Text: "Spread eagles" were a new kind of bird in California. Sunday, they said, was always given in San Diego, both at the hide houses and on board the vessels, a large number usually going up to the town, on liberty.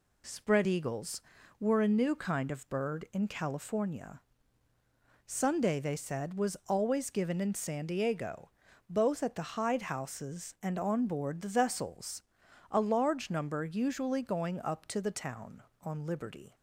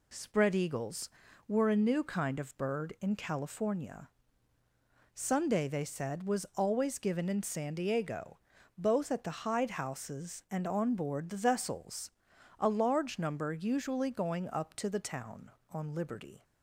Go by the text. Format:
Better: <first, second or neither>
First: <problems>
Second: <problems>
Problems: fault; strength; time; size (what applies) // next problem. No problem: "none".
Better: neither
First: none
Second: none